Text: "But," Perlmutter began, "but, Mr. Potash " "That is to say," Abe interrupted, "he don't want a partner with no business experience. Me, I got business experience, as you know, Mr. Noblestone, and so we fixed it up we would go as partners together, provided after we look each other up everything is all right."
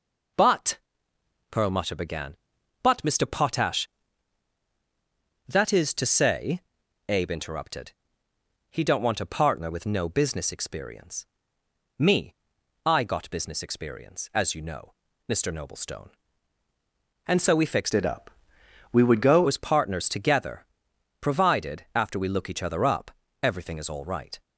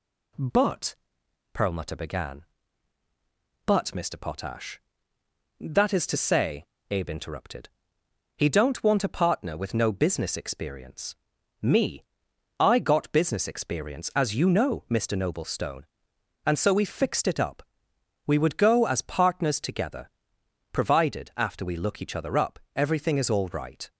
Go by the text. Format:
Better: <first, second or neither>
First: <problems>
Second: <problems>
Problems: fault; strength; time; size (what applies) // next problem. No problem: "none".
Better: second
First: changes voice from "it" to "go"; from 17.9 to 19.4 s; 1.5 s long // pauses between "up" and "we"; noticeable; at 18.3 s; 0.62 s long // pauses between "up" and "everything"; slight; at 23.1 s; 0.32 s long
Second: pauses between "up" and "we"; noticeable; at 17.6 s; 0.62 s long // pauses between "up" and "everything"; slight; at 22.5 s; 0.16 s long